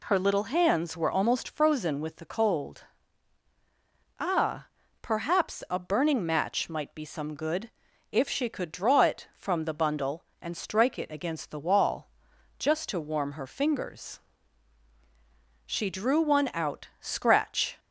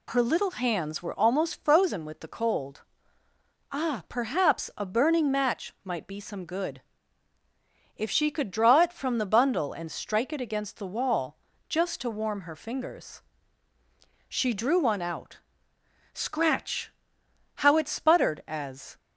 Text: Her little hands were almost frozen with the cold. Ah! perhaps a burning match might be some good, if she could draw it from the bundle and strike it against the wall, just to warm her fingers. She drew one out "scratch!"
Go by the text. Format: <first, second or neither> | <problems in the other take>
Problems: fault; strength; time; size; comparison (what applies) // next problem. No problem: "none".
first | pauses between "out" and "scratch"; noticeable; at 15.4 s; 0.74 s long // goes on to say "how it sputtered as"; from 17.5 s on; 1.4 s long